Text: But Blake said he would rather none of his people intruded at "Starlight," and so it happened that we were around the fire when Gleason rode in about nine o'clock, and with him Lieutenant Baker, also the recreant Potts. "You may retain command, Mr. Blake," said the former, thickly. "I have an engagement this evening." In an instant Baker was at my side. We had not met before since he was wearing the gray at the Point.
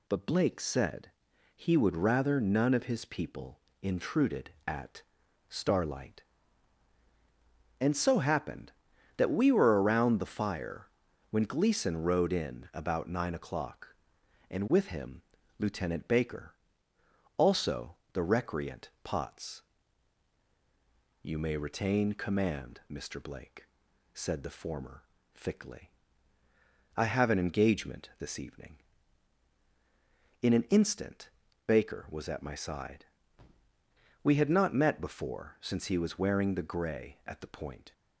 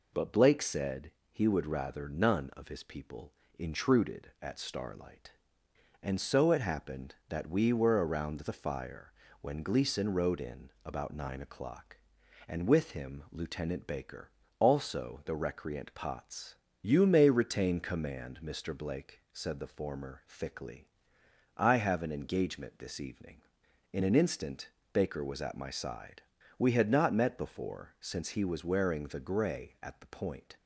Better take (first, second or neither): second